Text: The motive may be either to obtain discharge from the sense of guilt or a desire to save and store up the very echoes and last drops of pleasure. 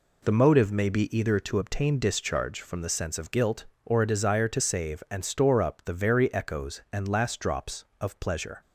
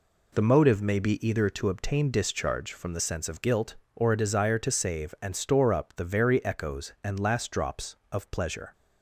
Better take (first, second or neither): neither